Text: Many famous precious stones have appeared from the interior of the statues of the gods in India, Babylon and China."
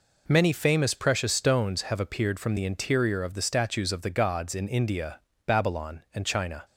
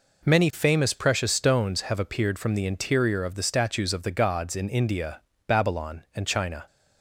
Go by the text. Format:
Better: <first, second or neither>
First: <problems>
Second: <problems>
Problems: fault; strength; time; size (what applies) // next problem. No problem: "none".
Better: neither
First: none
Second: none